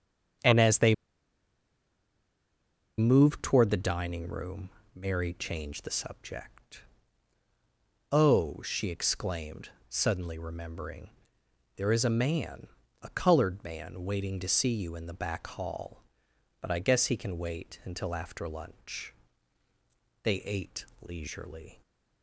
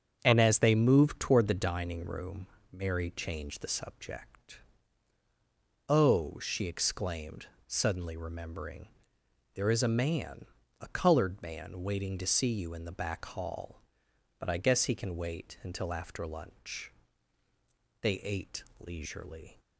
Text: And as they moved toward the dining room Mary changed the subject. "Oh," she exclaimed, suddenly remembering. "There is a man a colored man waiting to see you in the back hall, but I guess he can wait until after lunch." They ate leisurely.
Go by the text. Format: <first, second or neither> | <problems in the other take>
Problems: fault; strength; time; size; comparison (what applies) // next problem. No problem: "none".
second | starts louder than the rest; strong; until 3.4 s; 7.5 dB; strong in the second // pauses between "they" and "moved"; strong; at 0.9 s; 2.0 s long // pauses between "room" and "Mary"; slight; at 4.6 s; 0.24 s long; slight in the second // pauses between "man" and "a"; slight; at 12.6 s; 0.34 s long; slight in the second // pauses between "ate" and "leisurely"; slight; at 20.8 s; 0.16 s long; slight in the second